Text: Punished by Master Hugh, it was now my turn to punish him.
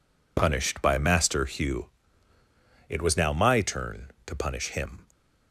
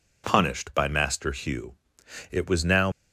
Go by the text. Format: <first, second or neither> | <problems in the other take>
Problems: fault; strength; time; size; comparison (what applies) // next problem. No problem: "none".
first | stops before "my turn to punish him"; at 2.9 s